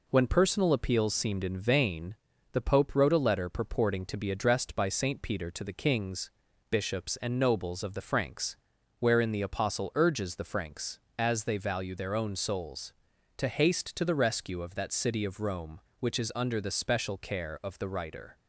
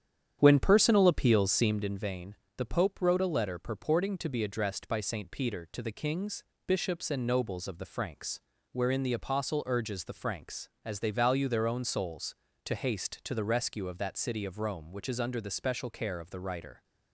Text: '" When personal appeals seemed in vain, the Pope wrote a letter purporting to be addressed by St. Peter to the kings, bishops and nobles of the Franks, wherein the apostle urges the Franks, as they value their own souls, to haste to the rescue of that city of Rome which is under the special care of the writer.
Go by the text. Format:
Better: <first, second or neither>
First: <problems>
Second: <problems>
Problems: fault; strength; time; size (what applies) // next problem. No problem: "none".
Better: first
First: none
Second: starts louder than the rest; strong; until 1.8 s; 9 dB